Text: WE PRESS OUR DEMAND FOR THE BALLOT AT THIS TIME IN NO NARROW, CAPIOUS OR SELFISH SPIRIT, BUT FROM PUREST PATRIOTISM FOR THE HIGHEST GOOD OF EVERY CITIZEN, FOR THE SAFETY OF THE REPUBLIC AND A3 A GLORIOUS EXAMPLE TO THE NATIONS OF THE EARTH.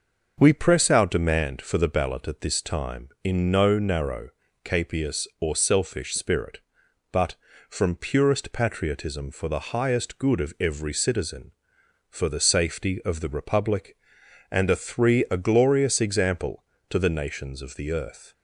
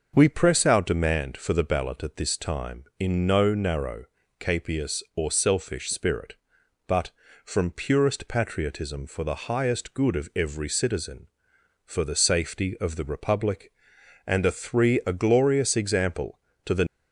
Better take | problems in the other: first | starts louder than the rest; noticeable; until 1.1 s; 6 dB; noticeable in the first // stops before "NATIONS OF THE EARTH"; at 16.8 s

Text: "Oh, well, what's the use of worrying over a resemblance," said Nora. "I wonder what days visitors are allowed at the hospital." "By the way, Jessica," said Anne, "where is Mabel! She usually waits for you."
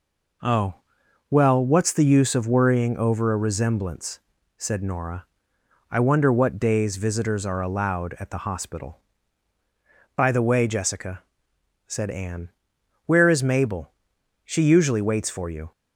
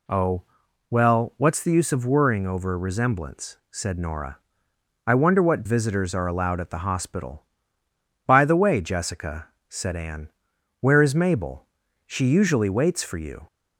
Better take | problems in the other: first | skips "days"; at 5.6 s

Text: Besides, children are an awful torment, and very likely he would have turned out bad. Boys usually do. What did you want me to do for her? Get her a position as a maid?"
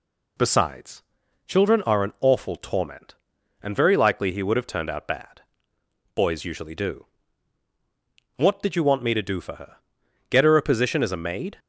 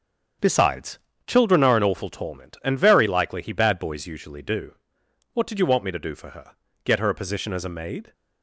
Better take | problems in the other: first | starts louder than the rest; strong; until 1.6 s; 7.5 dB // skips "would have turned out"; at 3.5 s

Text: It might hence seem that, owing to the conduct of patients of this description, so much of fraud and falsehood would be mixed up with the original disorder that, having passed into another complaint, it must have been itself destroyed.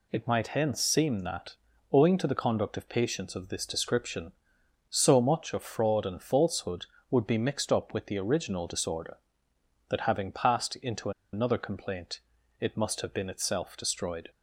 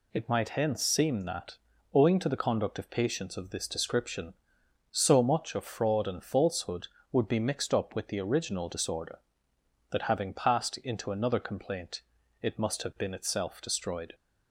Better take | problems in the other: second | pauses between "into" and "another"; slight; at 11.1 s; 0.22 s long

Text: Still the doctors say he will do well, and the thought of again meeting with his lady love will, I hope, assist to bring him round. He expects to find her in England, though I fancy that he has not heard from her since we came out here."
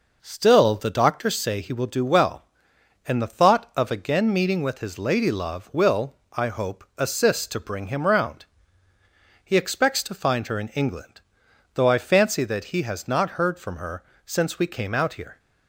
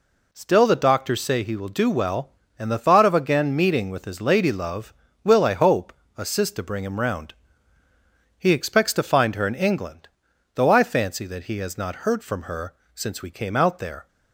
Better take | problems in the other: first | pauses between "her" and "since"; slight; at 12.7 s; 0.22 s long; slight in the first // says "there" for "here"; at 13.7 s

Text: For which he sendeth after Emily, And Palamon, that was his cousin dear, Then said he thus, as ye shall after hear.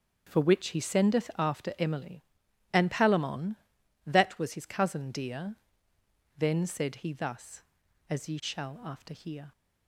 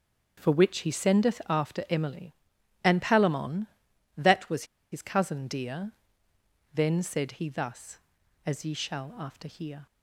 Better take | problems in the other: first | starts louder than the rest; until 1.4 s; 6.5 dB; also in the first // pauses between "was" and "his"; slight; at 4.6 s; 0.27 s long

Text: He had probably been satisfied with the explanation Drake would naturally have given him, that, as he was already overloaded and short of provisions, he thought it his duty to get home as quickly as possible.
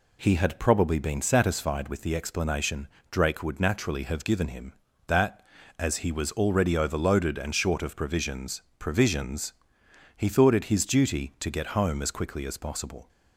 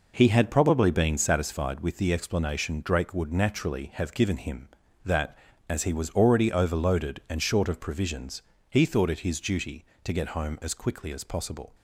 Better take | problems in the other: second | pauses between "explanation" and "Drake"; slight; at 2.8 s; 0.22 s long // says "provisions" twice; at 8.7 s

